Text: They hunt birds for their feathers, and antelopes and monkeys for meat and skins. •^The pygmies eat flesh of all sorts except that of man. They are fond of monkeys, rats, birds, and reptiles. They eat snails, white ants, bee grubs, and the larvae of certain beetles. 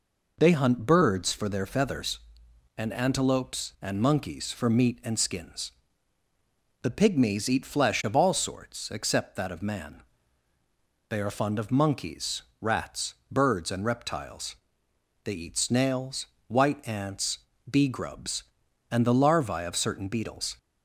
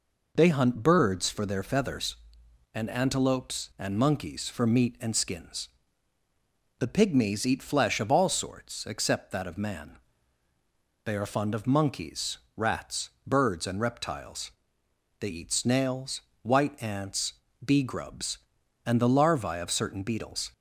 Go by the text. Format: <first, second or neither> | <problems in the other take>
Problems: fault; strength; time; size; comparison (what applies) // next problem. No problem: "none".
neither | none